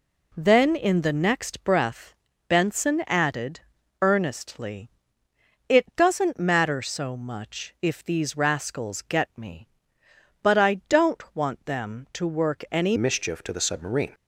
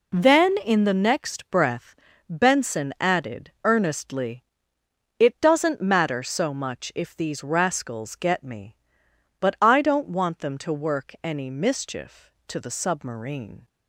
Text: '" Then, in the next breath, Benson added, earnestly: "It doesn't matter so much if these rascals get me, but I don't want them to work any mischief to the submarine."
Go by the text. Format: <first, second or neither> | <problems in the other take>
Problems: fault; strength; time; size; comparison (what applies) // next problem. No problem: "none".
second | changes voice at "mischief"; from 12.9 s on; 1.2 s long